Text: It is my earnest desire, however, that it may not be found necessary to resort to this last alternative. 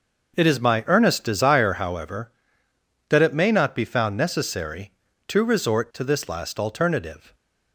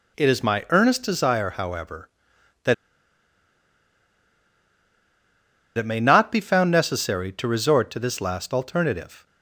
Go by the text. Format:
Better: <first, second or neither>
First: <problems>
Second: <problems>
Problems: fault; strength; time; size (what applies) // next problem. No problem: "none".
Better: first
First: none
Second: pauses between "that" and "it"; strong; at 2.7 s; 3.0 s long